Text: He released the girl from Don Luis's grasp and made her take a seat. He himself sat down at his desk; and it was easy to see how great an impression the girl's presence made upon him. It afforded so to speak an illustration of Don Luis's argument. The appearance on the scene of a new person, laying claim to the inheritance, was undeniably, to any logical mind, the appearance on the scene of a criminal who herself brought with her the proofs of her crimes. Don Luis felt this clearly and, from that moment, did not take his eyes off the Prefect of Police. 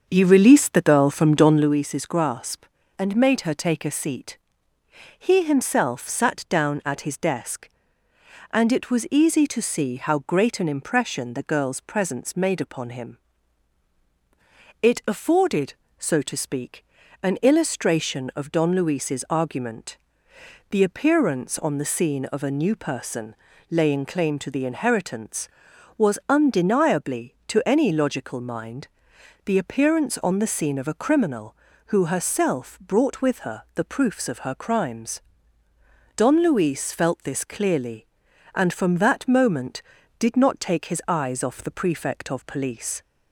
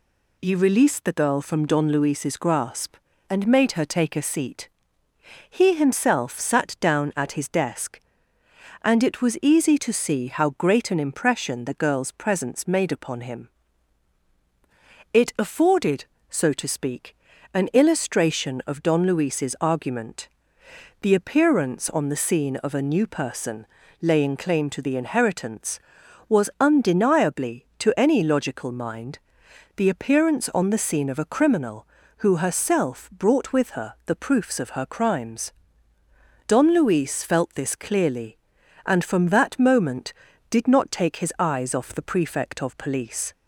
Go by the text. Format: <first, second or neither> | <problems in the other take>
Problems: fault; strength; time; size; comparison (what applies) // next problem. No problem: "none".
second | starts louder than the rest; until 1.7 s; 6.5 dB // pauses between "speak" and "an"; slight; at 16.8 s; 0.36 s long; slight in the second